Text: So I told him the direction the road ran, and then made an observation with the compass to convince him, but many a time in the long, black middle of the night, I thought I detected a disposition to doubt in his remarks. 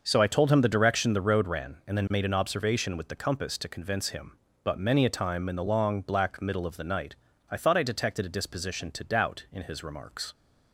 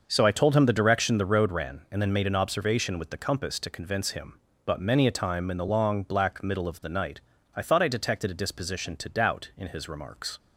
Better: neither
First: starts louder than the rest; noticeable; until 1.0 s; 6 dB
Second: starts louder than the rest; noticeable; until 1.0 s; 6 dB

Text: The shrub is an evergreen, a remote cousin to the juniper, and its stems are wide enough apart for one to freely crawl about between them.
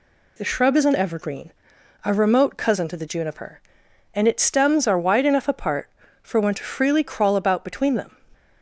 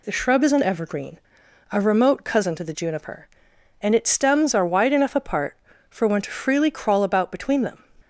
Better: neither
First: none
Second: none

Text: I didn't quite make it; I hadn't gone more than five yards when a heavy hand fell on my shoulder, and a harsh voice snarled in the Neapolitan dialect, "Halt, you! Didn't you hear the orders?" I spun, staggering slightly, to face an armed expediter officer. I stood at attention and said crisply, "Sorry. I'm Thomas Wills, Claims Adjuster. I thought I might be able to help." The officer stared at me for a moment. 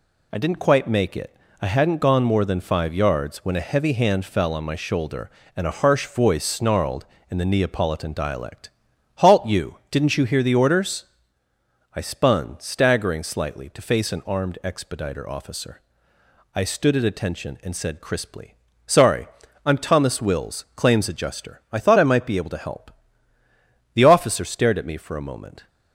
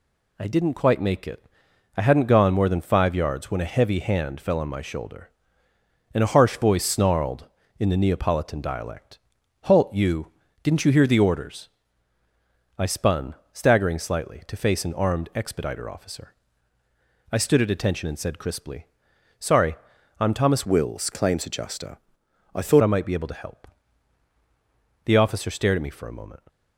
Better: first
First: none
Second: changes voice from "Wills" to "thought"; from 20.6 to 22.8 s; 2.2 s long

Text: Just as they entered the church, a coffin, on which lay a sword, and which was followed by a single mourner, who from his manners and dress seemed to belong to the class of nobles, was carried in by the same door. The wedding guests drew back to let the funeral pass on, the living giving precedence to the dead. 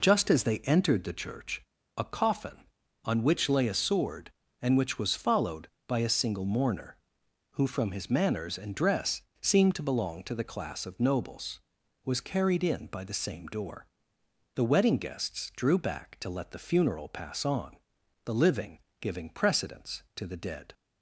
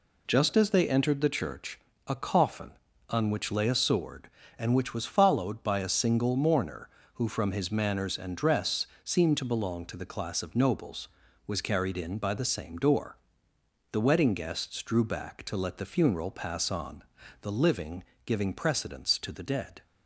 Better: neither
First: pauses between "dress" and "seemed"; slight; at 9.2 s; 0.20 s long // pauses between "living" and "giving"; slight; at 18.7 s; 0.22 s long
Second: pauses between "dress" and "seemed"; slight; at 8.8 s; 0.18 s long // pauses between "living" and "giving"; slight; at 18.0 s; 0.22 s long

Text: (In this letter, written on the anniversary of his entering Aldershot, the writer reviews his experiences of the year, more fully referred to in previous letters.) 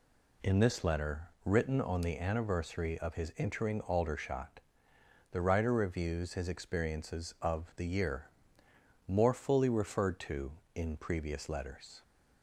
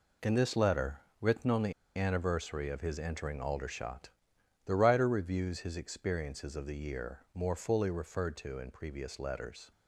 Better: first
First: none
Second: pauses between "the" and "anniversary"; slight; at 1.7 s; 0.23 s long

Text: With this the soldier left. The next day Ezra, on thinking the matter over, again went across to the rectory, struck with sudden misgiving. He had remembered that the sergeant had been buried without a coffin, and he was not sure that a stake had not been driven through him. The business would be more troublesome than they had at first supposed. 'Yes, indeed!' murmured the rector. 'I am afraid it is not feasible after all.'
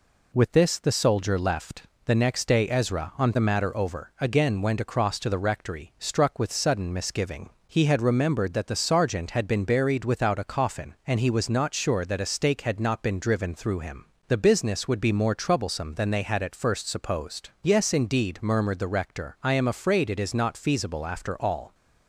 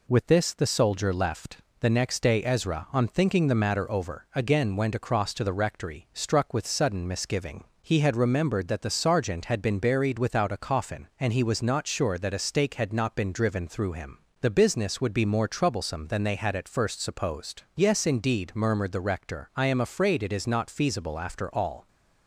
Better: second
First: skips "thinking"; at 3.3 s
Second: none

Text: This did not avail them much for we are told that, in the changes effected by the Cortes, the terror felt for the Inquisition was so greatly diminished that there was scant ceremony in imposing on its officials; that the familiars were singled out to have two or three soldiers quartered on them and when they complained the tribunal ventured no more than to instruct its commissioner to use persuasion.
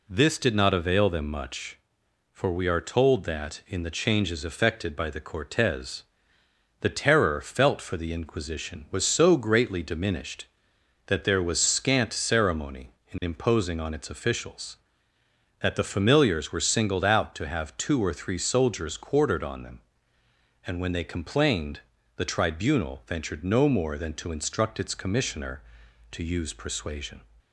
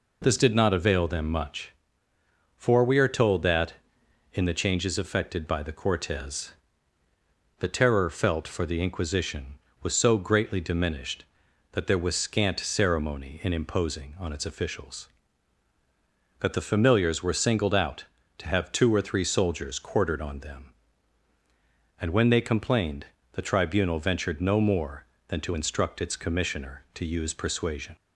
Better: neither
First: pauses between "complained" and "the"; slight; at 21.8 s; 0.36 s long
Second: pauses between "complained" and "the"; slight; at 23.0 s; 0.26 s long

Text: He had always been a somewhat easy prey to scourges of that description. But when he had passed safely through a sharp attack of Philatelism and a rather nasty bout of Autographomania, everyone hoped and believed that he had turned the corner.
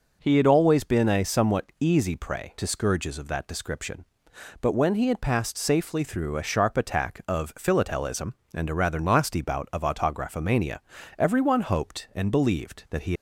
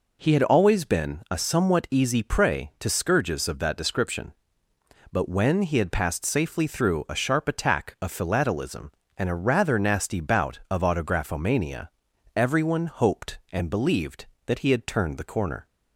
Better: second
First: stops before "had turned the corner"; at 13.1 s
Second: none

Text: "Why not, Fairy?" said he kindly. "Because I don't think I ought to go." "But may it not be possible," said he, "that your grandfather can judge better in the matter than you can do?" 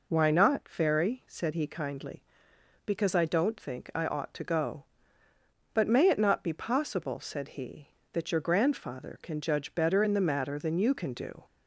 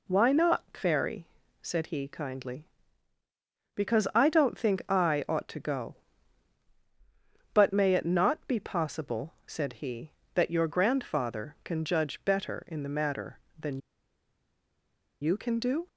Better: first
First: none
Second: pauses between "than" and "you"; strong; at 13.8 s; 1.4 s long

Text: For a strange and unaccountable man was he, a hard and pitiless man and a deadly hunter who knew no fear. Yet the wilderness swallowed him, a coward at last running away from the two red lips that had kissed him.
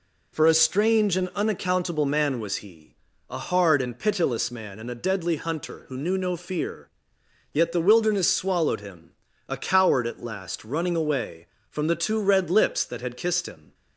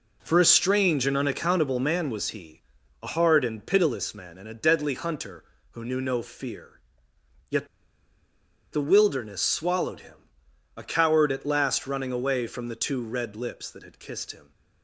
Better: first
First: none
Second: pauses between "Yet" and "the"; at 7.6 s; 1.0 s long

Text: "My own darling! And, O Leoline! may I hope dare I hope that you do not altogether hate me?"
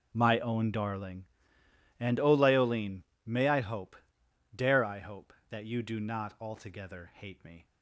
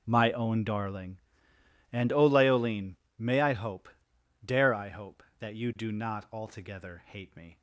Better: neither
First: pauses between "hope" and "dare"; noticeable; at 3.9 s; 0.60 s long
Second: pauses between "hope" and "dare"; noticeable; at 3.8 s; 0.58 s long

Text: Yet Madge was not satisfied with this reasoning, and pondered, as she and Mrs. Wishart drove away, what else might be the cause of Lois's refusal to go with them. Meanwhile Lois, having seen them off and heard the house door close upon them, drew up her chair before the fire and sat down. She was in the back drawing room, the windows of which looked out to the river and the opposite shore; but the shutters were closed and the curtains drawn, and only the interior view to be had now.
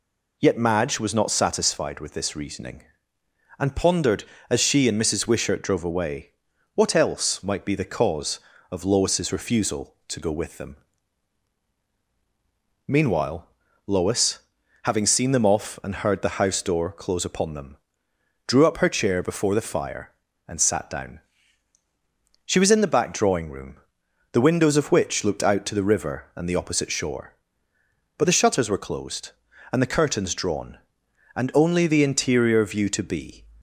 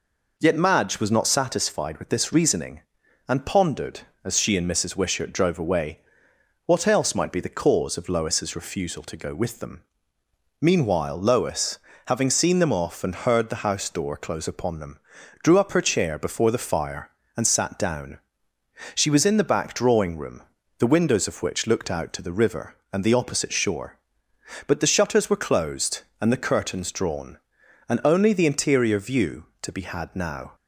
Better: second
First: pauses between "Meanwhile" and "Lois"; at 13.4 s; 0.38 s long // stops before "had now"; at 33.5 s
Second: none

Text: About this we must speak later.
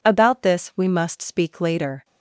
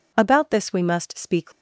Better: first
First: none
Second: stops before "later"; at 1.5 s

